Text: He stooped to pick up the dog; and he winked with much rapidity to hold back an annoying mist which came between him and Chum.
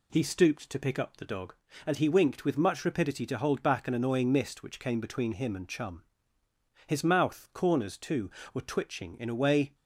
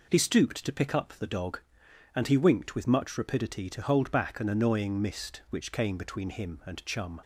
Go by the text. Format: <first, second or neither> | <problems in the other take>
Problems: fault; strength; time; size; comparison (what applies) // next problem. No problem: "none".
second | goes on to say "His mouth corners too were twitching in a way"; strong; from 6.8 s on; 2.8 s long